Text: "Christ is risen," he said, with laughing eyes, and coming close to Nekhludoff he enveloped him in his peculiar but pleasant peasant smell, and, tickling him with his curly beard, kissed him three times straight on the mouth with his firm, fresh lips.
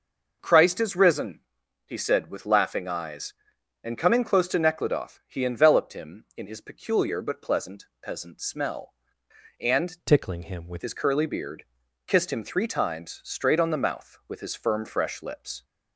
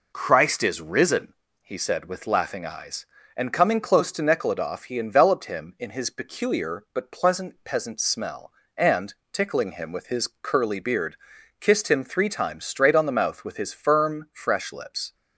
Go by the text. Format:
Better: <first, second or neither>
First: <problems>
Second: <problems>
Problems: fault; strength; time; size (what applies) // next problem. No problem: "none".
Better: second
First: changes voice from "tickling" to "with"; from 10.0 to 10.8 s; 0.8 s long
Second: none